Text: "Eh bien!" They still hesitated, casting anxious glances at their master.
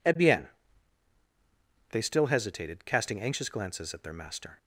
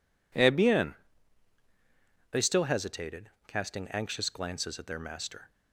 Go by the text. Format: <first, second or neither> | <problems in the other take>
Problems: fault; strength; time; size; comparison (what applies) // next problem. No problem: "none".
neither | none